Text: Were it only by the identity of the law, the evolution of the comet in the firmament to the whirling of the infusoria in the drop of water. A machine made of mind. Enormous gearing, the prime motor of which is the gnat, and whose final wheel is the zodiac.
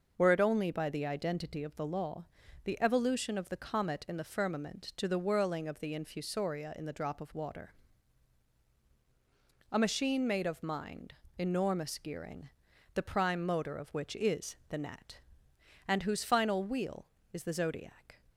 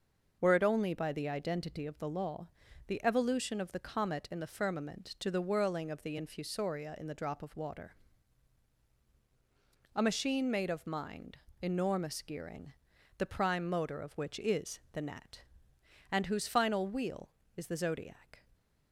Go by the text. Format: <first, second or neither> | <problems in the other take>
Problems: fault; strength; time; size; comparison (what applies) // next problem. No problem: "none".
neither | none